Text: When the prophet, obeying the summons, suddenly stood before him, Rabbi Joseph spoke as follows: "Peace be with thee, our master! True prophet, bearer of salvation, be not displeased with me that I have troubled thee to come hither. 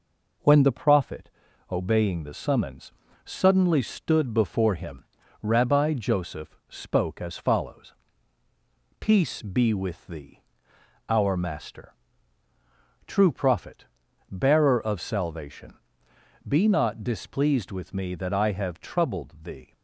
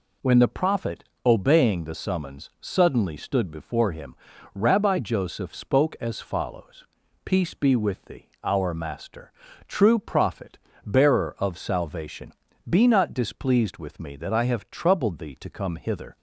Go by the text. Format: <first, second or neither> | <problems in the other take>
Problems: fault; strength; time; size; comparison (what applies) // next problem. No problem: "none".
second | stops before "to come hither"; at 19.7 s